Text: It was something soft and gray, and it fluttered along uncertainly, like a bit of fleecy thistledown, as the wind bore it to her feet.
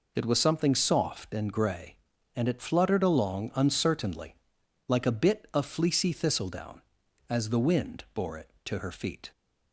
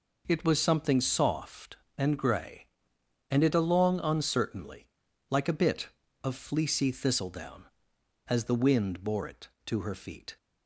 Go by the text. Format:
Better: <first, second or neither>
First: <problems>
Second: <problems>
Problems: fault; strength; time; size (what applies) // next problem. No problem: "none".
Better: first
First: none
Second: skips "fluttered"; at 3.5 s